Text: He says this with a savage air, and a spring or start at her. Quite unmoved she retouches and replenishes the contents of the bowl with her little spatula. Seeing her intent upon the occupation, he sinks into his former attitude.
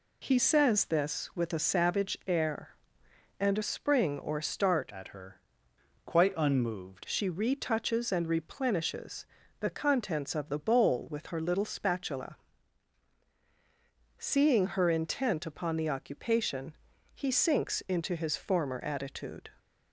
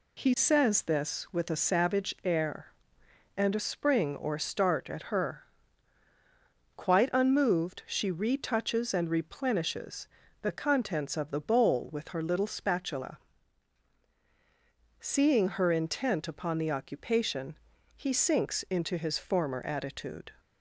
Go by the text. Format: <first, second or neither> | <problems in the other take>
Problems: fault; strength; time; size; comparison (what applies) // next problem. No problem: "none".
second | changes voice from "at" to "unmoved"; from 4.9 to 7.0 s; 2.1 s long // pauses between "replenishes" and "the"; slight; at 9.2 s; 0.34 s long; slight in the second